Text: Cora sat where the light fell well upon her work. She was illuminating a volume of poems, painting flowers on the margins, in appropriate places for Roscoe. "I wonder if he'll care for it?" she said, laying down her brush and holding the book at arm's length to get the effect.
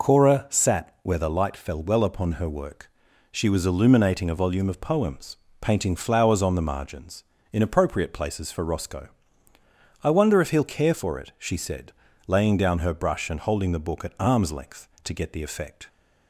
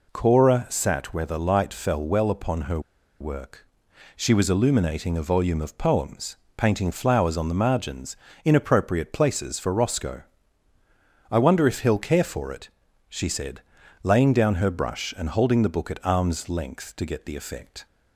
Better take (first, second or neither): first